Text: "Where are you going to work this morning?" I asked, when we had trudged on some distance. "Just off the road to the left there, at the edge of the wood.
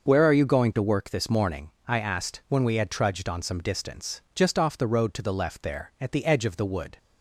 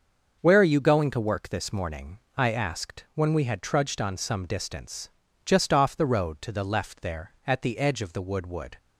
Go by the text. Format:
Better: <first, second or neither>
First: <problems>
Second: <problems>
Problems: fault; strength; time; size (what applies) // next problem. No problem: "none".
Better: first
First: starts louder than the rest; noticeable; until 1.1 s; 6 dB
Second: starts louder than the rest; until 1.4 s; 6 dB // says "wood" twice; at 8.4 s